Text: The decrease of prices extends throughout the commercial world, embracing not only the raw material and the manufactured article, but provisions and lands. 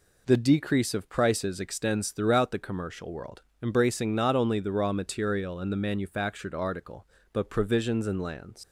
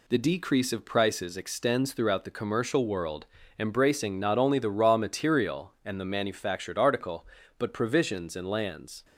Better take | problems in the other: second | leaves "lands" unfinished; at 8.6 s; 90 ms

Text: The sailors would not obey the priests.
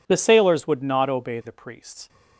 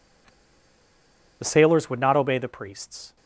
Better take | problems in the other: first | pauses between "The" and "sailors"; at 0.2 s; 1.1 s long

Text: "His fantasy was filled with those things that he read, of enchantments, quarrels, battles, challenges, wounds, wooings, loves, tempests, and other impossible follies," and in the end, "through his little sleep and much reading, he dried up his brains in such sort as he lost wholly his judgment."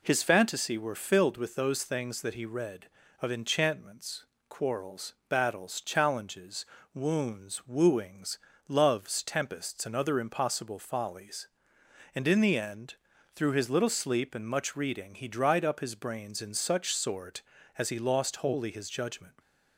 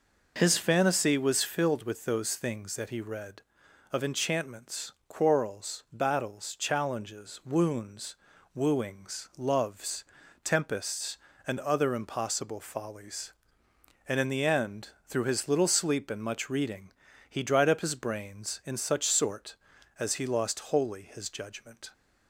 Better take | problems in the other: second | says "were" for "was"; at 0.7 s

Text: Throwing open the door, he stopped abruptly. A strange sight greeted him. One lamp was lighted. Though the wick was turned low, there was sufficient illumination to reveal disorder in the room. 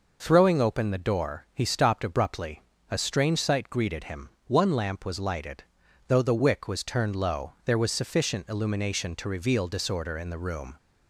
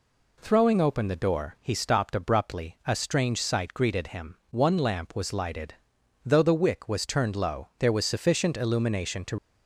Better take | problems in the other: first | stops before "reveal disorder in the room"; at 9.3 s

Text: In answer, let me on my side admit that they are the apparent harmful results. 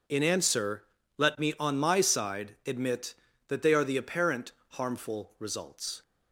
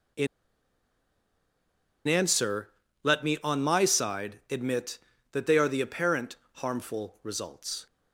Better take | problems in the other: first | pauses between "In" and "answer"; strong; at 0.2 s; 1.8 s long // pauses between "apparent" and "harmful"; slight; at 6.3 s; 0.16 s long; slight in the first

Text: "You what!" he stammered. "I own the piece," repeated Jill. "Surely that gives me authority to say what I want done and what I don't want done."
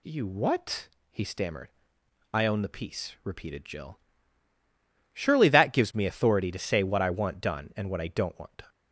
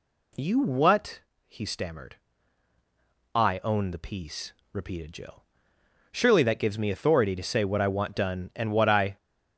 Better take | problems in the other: first | stops before "don't want done"; at 9.1 s

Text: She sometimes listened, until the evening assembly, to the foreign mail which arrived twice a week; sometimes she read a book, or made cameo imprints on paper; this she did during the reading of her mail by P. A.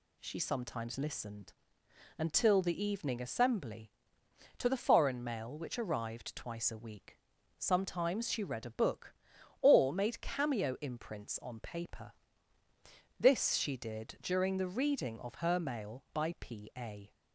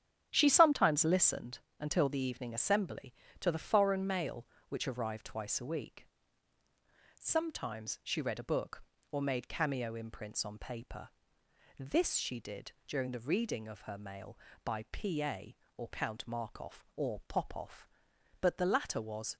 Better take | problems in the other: first | starts louder than the rest; strong; until 1.3 s; 9.5 dB // pauses between "did" and "during"; slight; at 12.7 s; 0.16 s long // goes on to say "or Count Markov or Popov but the latter was"; strong; from 15.7 s on; 3.5 s long

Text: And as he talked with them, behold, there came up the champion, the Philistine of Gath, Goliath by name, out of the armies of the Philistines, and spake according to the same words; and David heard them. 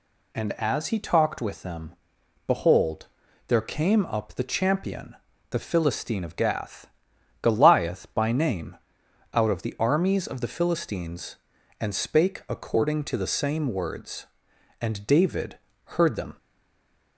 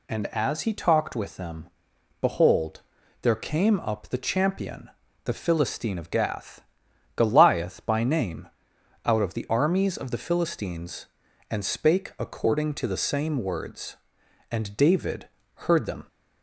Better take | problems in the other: second | pauses between "David" and "heard"; slight; at 15.5 s; 0.26 s long; slight in the second // stays silent after the last word; slight; from 16.3 s on; 0.8 s long

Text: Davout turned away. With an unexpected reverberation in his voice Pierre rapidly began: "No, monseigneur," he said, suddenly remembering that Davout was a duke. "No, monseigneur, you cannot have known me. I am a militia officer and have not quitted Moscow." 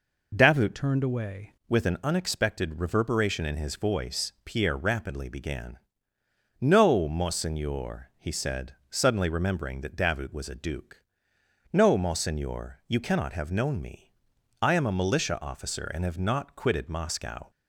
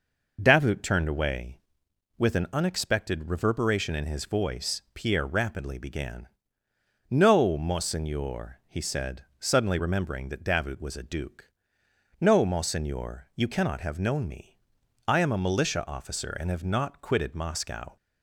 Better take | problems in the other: second | changes voice from "turned" to "away"; from 0.7 to 1.5 s; 0.8 s long

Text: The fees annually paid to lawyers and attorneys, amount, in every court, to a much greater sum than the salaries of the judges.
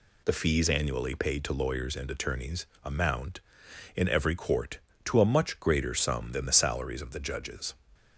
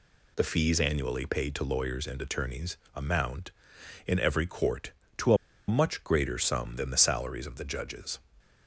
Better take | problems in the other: first | pauses between "a" and "much"; slight; at 5.3 s; 0.32 s long

